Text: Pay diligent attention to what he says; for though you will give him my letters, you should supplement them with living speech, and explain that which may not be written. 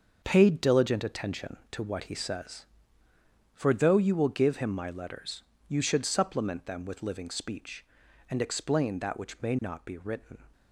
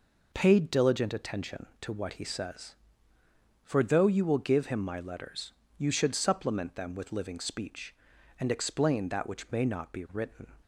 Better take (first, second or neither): second